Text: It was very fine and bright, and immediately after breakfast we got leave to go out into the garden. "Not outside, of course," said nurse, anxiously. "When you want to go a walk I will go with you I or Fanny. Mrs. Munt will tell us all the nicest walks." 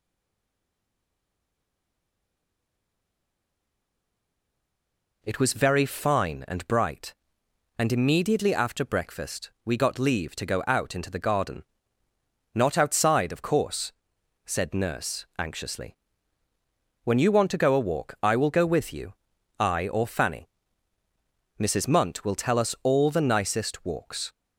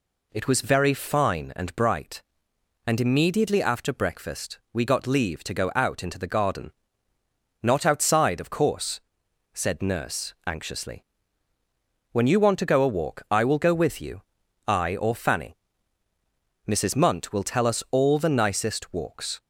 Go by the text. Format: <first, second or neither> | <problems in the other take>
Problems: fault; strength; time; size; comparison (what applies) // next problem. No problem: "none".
second | stays silent before the first word; strong; until 5.2 s; 5.2 s long // pauses between "you" and "I"; noticeable; at 19.1 s; 0.46 s long; noticeable in the second